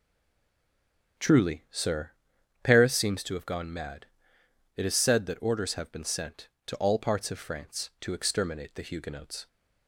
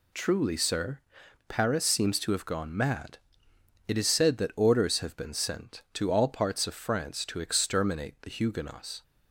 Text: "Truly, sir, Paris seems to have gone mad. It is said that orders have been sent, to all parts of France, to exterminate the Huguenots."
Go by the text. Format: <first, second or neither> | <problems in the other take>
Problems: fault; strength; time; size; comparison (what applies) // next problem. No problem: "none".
second | stays silent before the first word; noticeable; until 1.1 s; 1.1 s long // starts louder than the rest; strong; until 2.7 s; 8 dB